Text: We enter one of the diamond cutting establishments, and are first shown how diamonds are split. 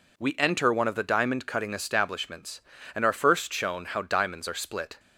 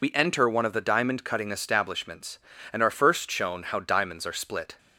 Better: first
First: none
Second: loses the start of "We"; at 0.0 s; 75 ms

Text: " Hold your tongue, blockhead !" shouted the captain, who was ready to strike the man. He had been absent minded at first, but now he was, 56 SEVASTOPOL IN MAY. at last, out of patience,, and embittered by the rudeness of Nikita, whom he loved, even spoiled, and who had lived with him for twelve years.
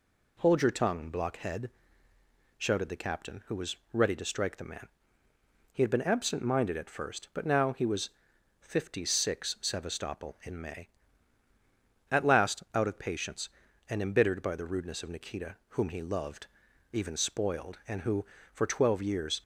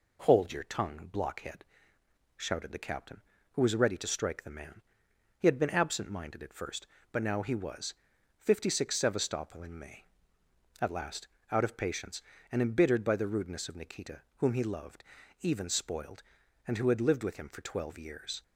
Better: second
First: pauses between "was" and "ready"; slight; at 3.7 s; 0.16 s long // skips "had lived with him"; at 18.3 s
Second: none

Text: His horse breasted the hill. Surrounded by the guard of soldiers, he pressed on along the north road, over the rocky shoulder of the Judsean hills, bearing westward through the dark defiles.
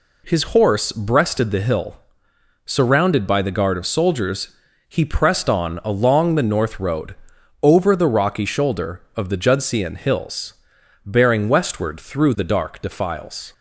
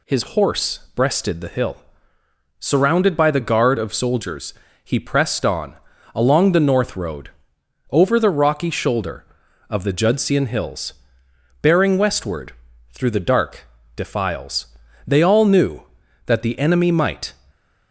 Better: first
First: none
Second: pauses between "on" and "along"; at 5.7 s; 0.40 s long // pauses between "westward" and "through"; at 12.5 s; 0.38 s long // pauses between "dark" and "defiles"; slight; at 13.6 s; 0.30 s long // goes on to say "They all knew that the enemy might"; strong; from 15.0 s on; 2.2 s long

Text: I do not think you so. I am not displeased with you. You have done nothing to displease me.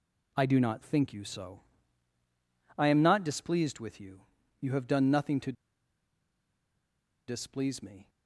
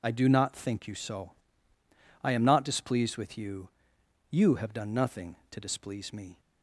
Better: second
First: pauses between "to" and "displease"; strong; at 5.5 s; 1.7 s long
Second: none

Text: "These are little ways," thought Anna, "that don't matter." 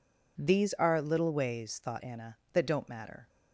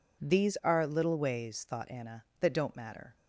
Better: neither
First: none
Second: none

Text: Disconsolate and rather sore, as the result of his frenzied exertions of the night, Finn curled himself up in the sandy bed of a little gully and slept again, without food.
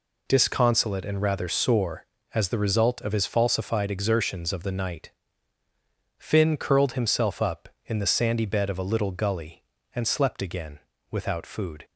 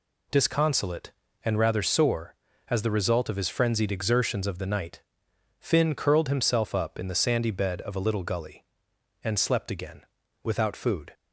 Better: second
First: says "falsified" for "frenzied"; at 3.2 s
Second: none

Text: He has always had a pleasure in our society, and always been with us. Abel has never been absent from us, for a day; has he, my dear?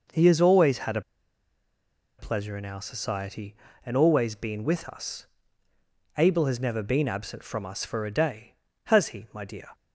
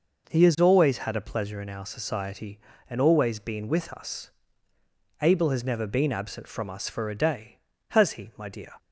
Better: second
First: pauses between "a" and "pleasure"; at 1.0 s; 1.1 s long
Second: none

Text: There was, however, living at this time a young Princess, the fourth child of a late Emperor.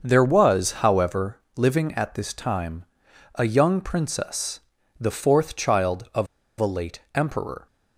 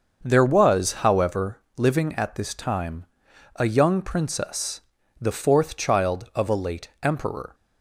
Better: second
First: starts louder than the rest; until 1.1 s; 6.5 dB // pauses between "time" and "a"; noticeable; at 2.8 s; 0.50 s long // pauses between "of" and "a"; slight; at 6.2 s; 0.31 s long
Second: starts louder than the rest; until 1.3 s; 6.5 dB // pauses between "time" and "a"; noticeable; at 3.0 s; 0.50 s long

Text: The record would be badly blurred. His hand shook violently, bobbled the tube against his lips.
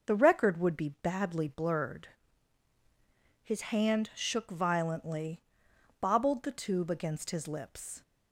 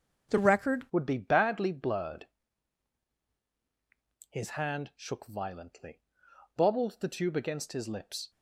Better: first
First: none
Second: starts louder than the rest; until 1.3 s; 7 dB // changes voice at "would"; from 0.9 s on; 7.4 s long

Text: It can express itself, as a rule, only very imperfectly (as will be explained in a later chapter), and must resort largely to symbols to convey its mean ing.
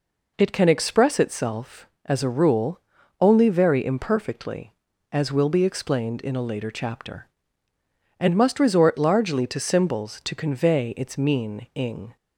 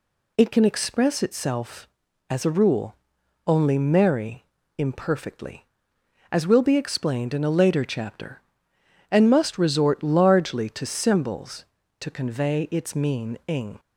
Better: first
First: none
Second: says "merry" for "very"; at 3.7 s

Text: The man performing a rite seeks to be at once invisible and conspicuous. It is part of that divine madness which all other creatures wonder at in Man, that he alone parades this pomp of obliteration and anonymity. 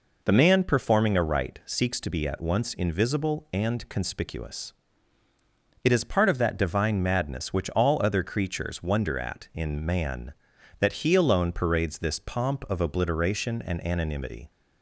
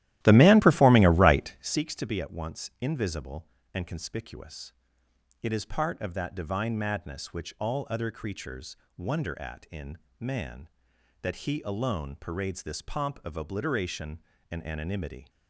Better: first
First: none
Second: starts louder than the rest; strong; until 1.8 s; 14 dB // pauses between "creatures" and "wonder"; slight; at 8.7 s; 0.22 s long // pauses between "in" and "Man"; slight; at 9.9 s; 0.22 s long

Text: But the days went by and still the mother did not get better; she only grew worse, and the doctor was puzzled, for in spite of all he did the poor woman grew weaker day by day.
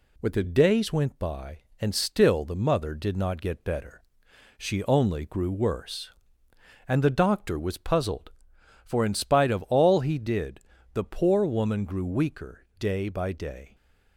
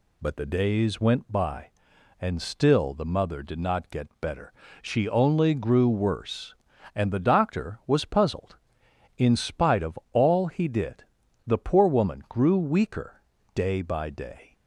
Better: first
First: pauses between "did" and "the"; slight; at 10.5 s; 0.36 s long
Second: skips "for"; at 8.8 s // pauses between "did" and "the"; at 11.0 s; 0.44 s long // pauses between "weaker" and "day"; slight; at 13.2 s; 0.32 s long

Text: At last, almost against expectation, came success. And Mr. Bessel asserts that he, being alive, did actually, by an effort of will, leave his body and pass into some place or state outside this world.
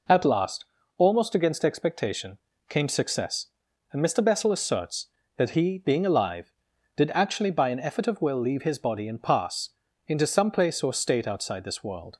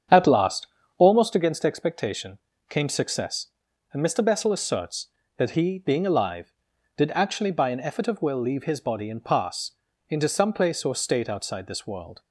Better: first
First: pauses between "pass" and "into"; slight; at 9.7 s; 0.36 s long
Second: starts louder than the rest; strong; until 1.4 s; 8 dB // pauses between "pass" and "into"; slight; at 9.7 s; 0.36 s long

